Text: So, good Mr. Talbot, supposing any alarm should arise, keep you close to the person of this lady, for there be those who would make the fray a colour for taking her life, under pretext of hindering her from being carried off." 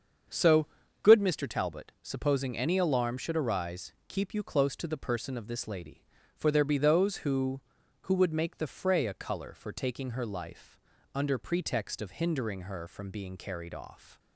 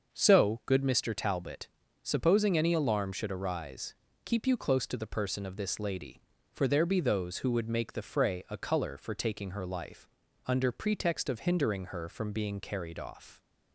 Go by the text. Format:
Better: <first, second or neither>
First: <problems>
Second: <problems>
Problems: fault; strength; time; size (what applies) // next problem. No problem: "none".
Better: second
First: starts louder than the rest; until 1.6 s; 7 dB // says "who" twice; at 8.0 s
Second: starts louder than the rest; until 1.1 s; 6.5 dB